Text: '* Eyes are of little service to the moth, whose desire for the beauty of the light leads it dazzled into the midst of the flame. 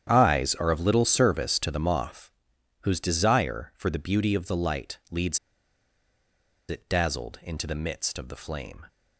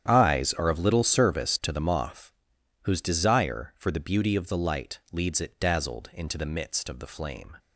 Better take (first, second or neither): second